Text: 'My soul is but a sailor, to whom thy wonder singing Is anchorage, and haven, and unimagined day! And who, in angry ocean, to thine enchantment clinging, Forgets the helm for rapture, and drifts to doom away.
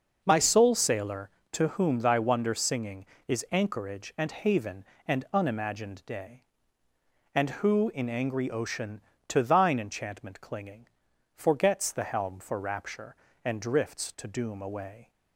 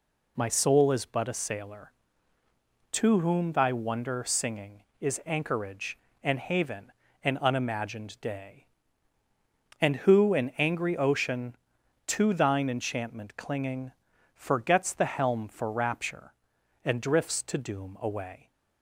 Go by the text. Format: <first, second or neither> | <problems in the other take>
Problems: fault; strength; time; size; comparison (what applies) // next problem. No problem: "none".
second | starts louder than the rest; noticeable; until 1.2 s; 6 dB // skips "is but a"; at 0.7 s